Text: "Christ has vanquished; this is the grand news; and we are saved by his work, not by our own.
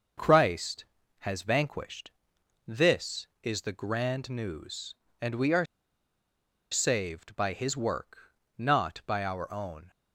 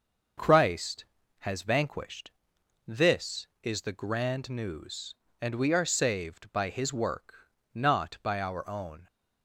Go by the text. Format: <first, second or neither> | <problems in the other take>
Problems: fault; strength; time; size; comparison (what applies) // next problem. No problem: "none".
second | starts louder than the rest; noticeable; until 1.5 s; 6 dB; noticeable in the second // pauses between "are" and "saved"; at 5.6 s; 1.0 s long